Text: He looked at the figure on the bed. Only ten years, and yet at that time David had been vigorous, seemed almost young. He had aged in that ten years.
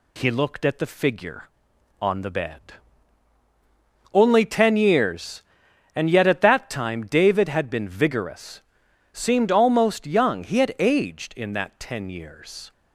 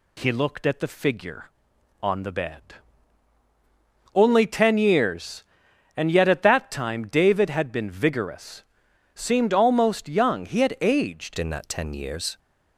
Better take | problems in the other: first | changes voice at "in"; from 11.3 s on; 1.0 s long

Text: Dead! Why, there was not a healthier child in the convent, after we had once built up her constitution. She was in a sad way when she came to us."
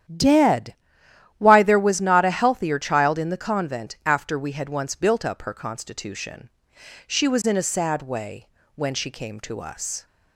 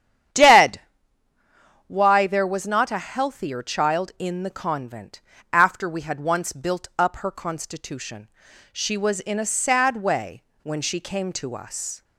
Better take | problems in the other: neither | starts louder than the rest; strong; the same in both // pauses between "way" and "when"; slight; the same in both

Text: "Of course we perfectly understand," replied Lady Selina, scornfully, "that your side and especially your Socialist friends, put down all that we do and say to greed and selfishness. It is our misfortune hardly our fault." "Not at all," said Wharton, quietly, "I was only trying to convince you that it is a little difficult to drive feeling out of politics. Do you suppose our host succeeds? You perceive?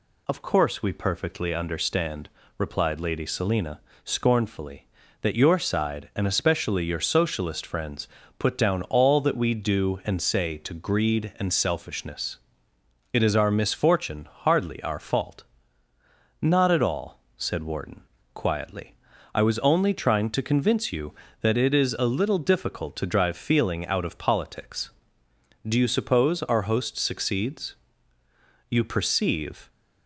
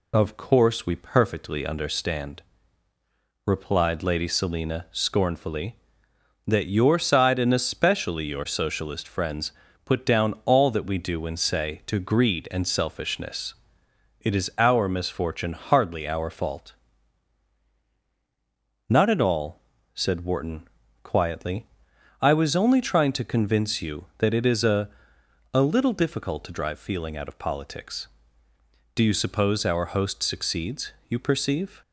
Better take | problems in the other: first | says "a" twice; at 25.5 s

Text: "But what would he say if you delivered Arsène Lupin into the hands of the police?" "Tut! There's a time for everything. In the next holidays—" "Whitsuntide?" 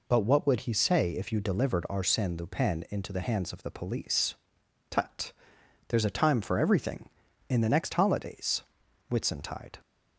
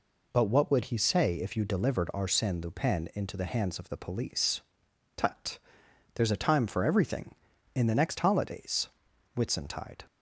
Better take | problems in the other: neither | none

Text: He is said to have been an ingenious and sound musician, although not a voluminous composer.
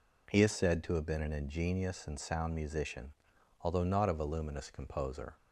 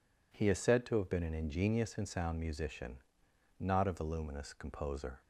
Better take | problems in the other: first | skips "although"; at 3.3 s

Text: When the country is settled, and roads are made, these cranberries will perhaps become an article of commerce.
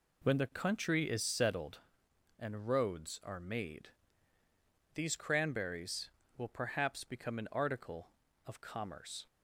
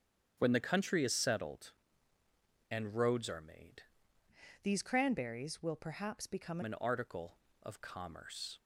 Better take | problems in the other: first | starts louder than the rest; strong; until 1.3 s; 8.5 dB // changes voice from "these" to "become"; from 4.6 to 6.6 s; 2.0 s long

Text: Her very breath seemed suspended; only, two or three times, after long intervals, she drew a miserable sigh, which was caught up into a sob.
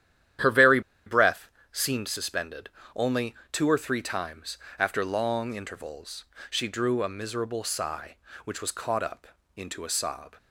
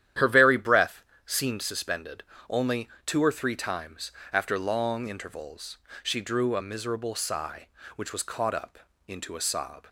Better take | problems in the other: second | starts louder than the rest; strong; until 1.9 s; 11 dB; strong in the second // pauses between "very" and "breath"; slight; at 0.7 s; 0.26 s long // pauses between "breath" and "seemed"; slight; at 1.4 s; 0.24 s long; slight in the second // pauses between "up" and "into"; slight; at 9.2 s; 0.30 s long; slight in the second

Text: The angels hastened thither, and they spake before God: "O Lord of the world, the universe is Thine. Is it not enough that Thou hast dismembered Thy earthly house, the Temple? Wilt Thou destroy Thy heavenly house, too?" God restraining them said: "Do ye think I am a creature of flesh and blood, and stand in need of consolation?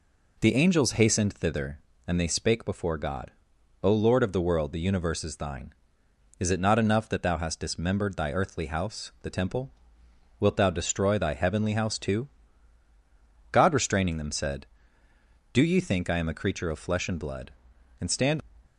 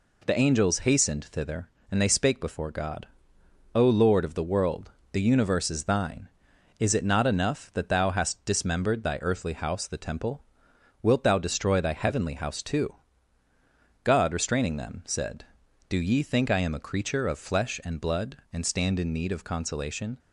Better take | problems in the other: second | stops before "in need of consolation"; at 18.6 s

